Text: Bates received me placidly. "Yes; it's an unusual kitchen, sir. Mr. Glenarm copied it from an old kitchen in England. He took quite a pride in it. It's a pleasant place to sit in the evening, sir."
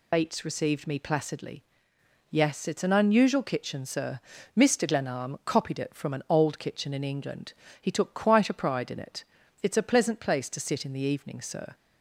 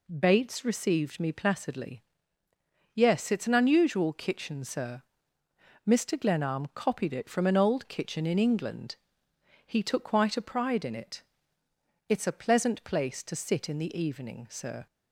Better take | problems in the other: second | loses the start of "Bates"; at 0.1 s; 70 ms

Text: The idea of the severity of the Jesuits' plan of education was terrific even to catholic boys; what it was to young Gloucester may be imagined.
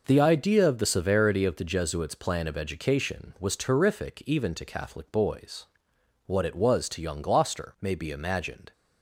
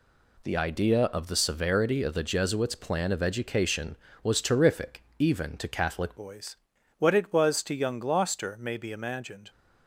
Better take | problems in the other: first | pauses between "terrific" and "even"; slight; at 5.0 s; 0.16 s long // changes voice at "boys"; from 6.1 s on; 3.4 s long

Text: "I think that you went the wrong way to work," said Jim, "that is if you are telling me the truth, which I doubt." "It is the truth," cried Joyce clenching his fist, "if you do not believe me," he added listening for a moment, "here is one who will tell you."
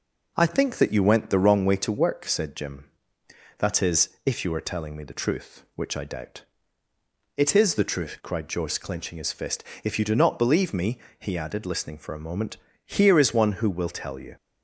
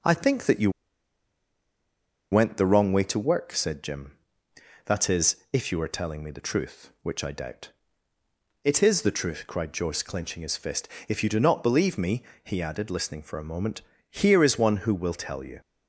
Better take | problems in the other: first | pauses between "you" and "went"; strong; at 0.7 s; 1.6 s long // pauses between "is" and "if"; slight; at 5.3 s; 0.16 s long; slight in the first

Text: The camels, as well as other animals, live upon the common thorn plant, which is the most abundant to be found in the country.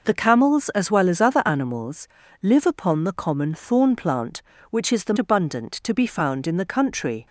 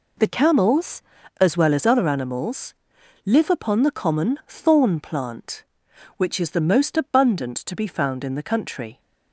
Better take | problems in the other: second | skips "most"; at 5.1 s

